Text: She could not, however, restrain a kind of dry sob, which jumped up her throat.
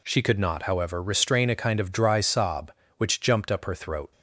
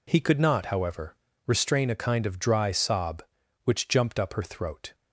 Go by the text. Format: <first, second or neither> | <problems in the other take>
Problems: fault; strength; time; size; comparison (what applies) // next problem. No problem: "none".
first | says "He" for "She"; at 0.0 s